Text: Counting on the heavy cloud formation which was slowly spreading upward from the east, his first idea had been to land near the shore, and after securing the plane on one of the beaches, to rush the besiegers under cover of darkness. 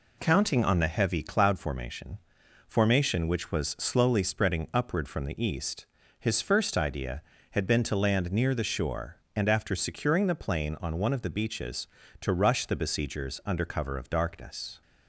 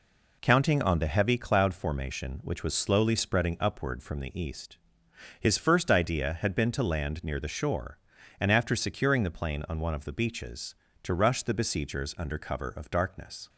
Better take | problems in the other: second | says "formation" twice; at 2.6 s

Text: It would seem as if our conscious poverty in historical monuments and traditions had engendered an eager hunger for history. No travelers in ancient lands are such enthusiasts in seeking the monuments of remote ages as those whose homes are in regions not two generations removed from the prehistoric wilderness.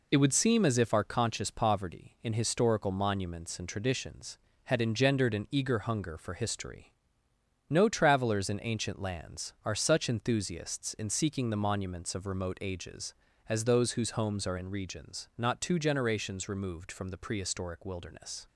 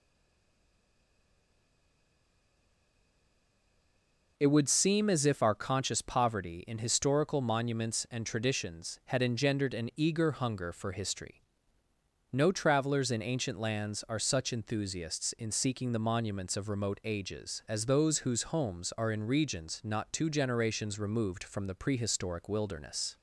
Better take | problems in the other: first | stays silent before the first word; strong; until 4.3 s; 4.3 s long

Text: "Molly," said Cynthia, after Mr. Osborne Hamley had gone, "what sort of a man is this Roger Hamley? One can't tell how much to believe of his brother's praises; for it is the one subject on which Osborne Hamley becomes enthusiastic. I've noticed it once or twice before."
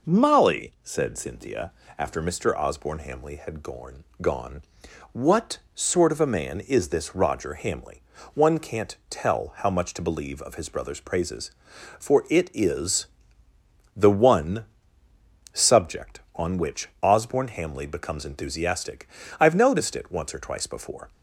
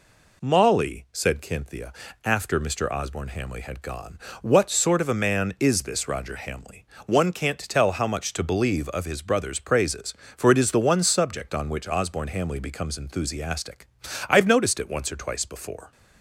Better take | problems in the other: second | says "gone" twice; at 4.2 s // pauses between "what" and "sort"; slight; at 5.5 s; 0.16 s long // pauses between "is" and "the"; noticeable; at 13.0 s; 0.90 s long // pauses between "one" and "subject"; noticeable; at 14.6 s; 0.88 s long

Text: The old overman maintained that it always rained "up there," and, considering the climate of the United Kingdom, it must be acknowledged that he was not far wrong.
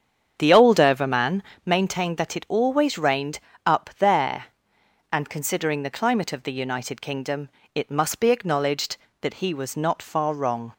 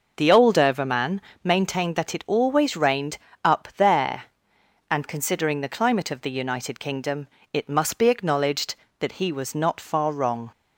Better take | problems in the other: second | starts louder than the rest; strong; until 1.7 s; 7.5 dB // pauses between "overman" and "maintained"; slight; at 1.4 s; 0.22 s long; slight in the second // pauses between "rained" and "up"; slight; at 3.3 s; 0.26 s long; slight in the second

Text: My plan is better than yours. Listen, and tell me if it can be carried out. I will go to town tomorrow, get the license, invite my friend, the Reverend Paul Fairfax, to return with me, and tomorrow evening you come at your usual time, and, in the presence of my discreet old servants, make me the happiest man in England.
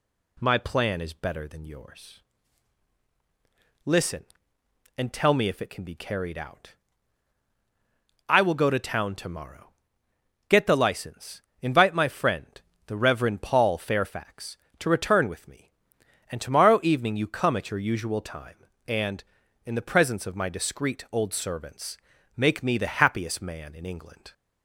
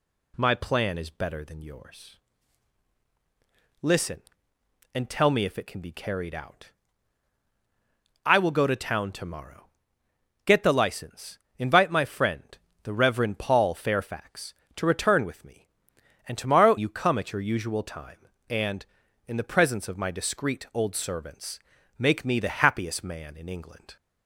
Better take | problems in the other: first | skips "evening"; at 16.7 s

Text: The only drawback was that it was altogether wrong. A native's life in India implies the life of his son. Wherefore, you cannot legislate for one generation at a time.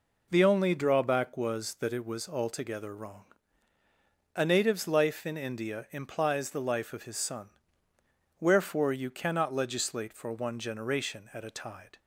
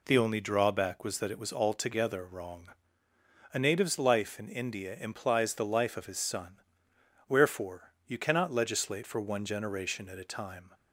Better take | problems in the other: second | says "tide" for "time"; at 11.5 s

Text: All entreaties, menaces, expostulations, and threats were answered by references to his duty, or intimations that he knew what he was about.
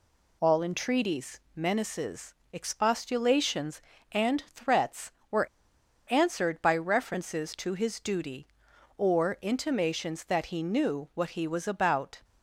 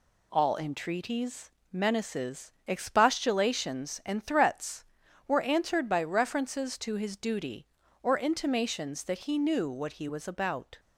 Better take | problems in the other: second | pauses between "were" and "answered"; noticeable; at 5.4 s; 0.61 s long

